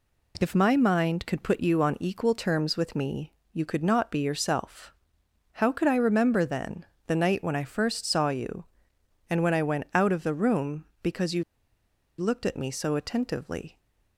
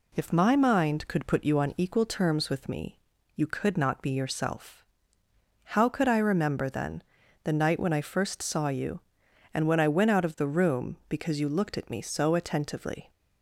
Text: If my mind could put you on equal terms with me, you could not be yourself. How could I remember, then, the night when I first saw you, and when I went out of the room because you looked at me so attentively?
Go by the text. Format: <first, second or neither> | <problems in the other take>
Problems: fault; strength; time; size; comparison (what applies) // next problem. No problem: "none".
second | pauses between "you" and "looked"; noticeable; at 11.4 s; 0.76 s long